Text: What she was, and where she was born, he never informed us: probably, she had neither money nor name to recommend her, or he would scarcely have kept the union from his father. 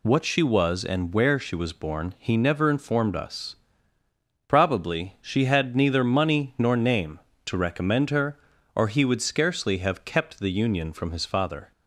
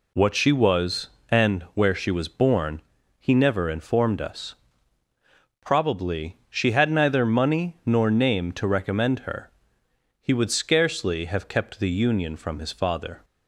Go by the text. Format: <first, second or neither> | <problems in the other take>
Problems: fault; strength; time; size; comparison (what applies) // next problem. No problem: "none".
first | skips "or"; at 9.8 s